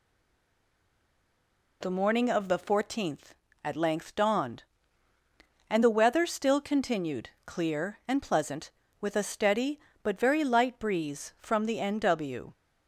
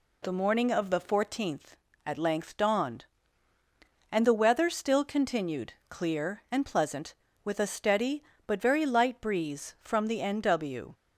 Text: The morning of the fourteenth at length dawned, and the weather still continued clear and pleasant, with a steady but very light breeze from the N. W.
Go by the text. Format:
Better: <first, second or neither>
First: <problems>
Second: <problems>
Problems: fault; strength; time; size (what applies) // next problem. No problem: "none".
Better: second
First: stays silent before the first word; noticeable; until 1.8 s; 1.8 s long // pauses between "continued" and "clear"; slight; at 7.2 s; 0.16 s long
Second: pauses between "continued" and "clear"; slight; at 5.7 s; 0.16 s long